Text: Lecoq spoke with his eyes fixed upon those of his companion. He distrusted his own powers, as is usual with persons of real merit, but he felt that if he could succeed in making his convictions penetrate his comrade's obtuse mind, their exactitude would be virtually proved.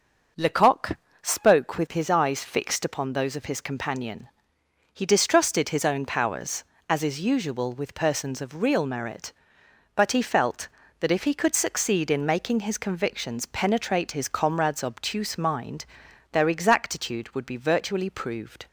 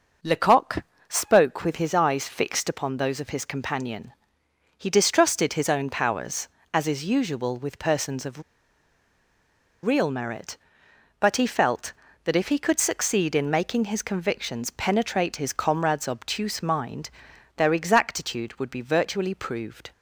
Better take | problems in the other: first | starts louder than the rest; noticeable; until 1.4 s; 6 dB; also in the first // pauses between "Lecoq" and "spoke"; slight; at 0.8 s; 0.26 s long; slight in the first // pauses between "of" and "real"; strong; at 8.4 s; 1.4 s long

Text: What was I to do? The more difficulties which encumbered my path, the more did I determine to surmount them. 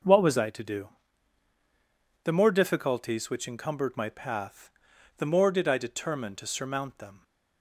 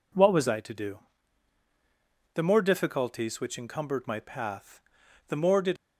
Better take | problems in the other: first | stops before "I determine to surmount them"; at 5.7 s

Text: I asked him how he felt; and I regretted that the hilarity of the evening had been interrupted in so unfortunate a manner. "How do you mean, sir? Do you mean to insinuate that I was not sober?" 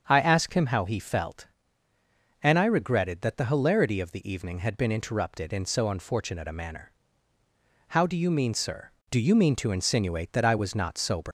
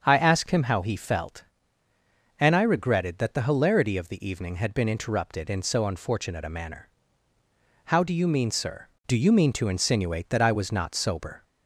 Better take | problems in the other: second | starts louder than the rest; until 1.0 s; 7 dB; also in the second // leaves "sober" unfinished; at 11.2 s; 150 ms

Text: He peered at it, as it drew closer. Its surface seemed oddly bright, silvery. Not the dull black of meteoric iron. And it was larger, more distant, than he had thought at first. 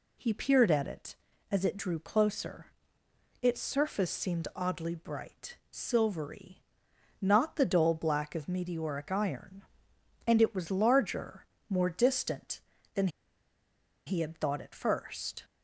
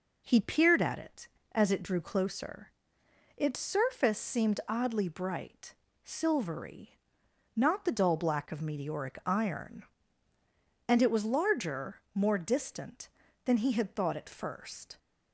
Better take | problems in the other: second | pauses between "than" and "he"; at 13.0 s; 1.0 s long

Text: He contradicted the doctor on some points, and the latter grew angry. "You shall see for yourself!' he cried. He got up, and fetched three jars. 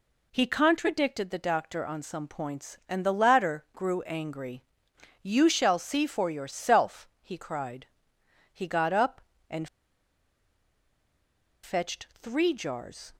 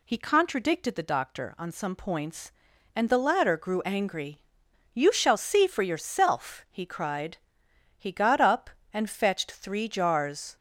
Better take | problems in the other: second | pauses between "and" and "fetched"; strong; at 9.6 s; 1.9 s long

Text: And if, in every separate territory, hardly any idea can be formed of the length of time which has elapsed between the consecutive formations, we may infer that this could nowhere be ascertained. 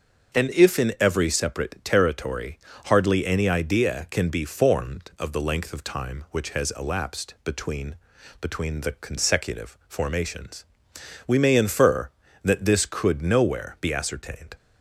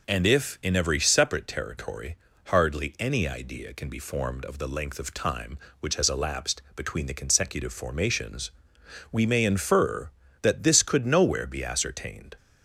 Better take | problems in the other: second | starts louder than the rest; until 1.4 s; 6.5 dB // says "between" twice; at 8.3 s

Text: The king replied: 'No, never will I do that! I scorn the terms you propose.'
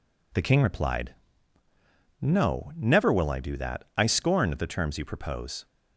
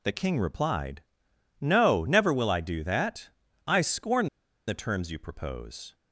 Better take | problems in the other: first | pauses between "scorn" and "the"; at 4.2 s; 0.40 s long

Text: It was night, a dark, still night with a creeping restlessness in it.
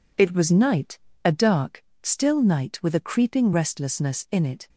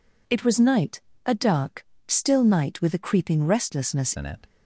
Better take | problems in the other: first | changes voice at "in"; from 4.1 s on; 0.3 s long

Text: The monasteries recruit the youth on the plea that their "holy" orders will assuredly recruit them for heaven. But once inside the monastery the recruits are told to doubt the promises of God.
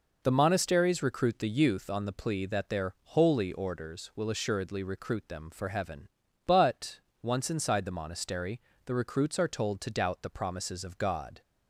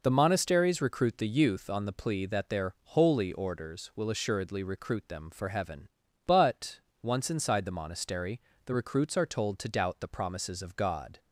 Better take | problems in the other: neither | pauses between "But" and "once"; slight; the same in both // pauses between "monastery" and "the"; slight; the same in both

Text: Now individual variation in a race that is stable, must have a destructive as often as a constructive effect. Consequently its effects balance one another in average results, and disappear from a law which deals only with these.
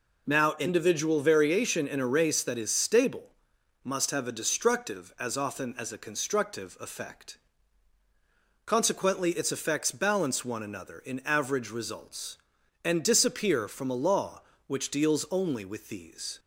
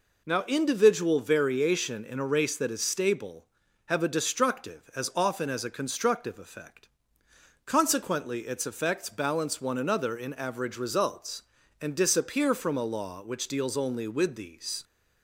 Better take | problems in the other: first | skips "must"; at 3.6 s

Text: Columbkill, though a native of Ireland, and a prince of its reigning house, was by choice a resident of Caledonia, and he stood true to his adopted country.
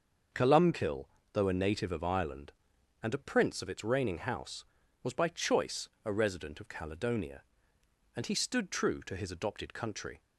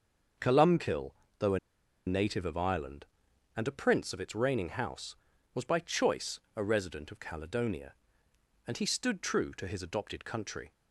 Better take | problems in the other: first | starts louder than the rest; until 2.1 s; 6.5 dB; also in the first // pauses between "a" and "native"; noticeable; at 1.5 s; 0.48 s long // pauses between "choice" and "a"; slight; at 6.3 s; 0.16 s long; slight in the first

